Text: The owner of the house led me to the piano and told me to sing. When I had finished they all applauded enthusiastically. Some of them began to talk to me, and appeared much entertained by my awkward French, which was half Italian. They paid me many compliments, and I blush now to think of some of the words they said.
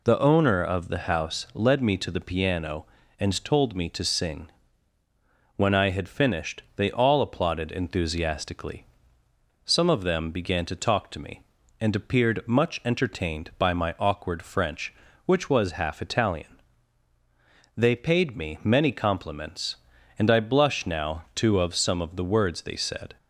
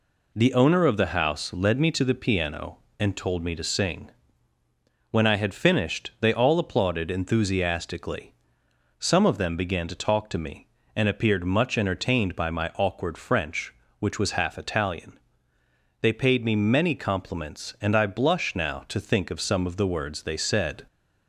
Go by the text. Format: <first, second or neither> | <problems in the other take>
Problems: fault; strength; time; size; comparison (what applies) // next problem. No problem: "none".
second | skips "think"; at 21.5 s